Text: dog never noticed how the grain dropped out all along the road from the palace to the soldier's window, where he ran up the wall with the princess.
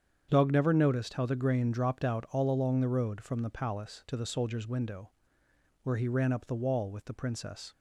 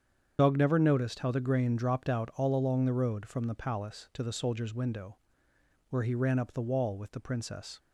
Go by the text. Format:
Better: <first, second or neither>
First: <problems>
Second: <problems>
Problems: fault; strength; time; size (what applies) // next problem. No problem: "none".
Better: first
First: starts louder than the rest; strong; until 1.3 s; 8 dB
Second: loses the start of "dog"; at 0.3 s; 40 ms // starts louder than the rest; strong; until 1.4 s; 8 dB